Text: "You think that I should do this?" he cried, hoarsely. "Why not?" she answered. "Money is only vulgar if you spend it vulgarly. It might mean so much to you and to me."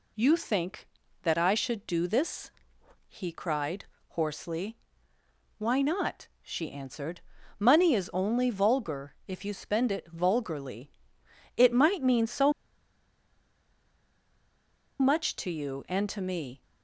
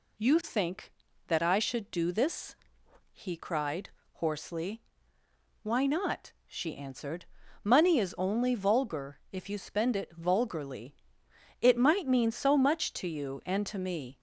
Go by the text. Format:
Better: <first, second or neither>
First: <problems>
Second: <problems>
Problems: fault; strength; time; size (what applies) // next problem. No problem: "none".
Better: second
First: pauses between "so" and "much"; strong; at 12.5 s; 2.4 s long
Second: none